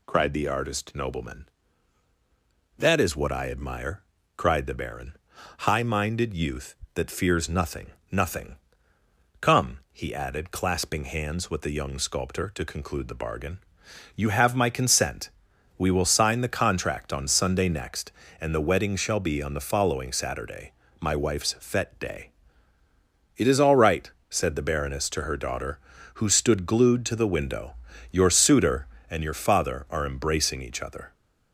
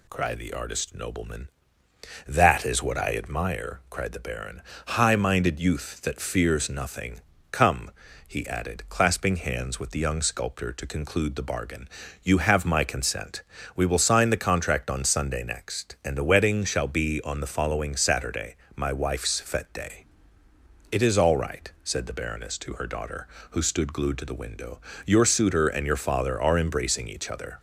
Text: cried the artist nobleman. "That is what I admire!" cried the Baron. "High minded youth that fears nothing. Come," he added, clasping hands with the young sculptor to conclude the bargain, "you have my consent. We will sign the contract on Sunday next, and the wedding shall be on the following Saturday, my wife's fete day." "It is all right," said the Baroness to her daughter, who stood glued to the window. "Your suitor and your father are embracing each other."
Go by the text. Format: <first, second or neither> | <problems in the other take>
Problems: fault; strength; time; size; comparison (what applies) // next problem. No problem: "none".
second | says "nothing" twice; at 8.1 s